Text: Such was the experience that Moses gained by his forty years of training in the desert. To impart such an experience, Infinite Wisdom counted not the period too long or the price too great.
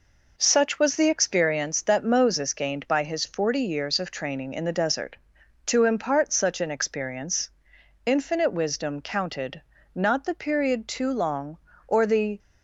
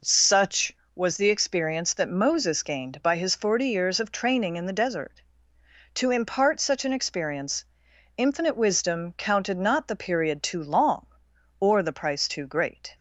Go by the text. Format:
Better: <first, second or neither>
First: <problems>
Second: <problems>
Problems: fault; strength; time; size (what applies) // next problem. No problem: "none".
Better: second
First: pauses between "counted" and "not"; slight; at 9.6 s; 0.32 s long // stops before "price too great"; at 12.3 s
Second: none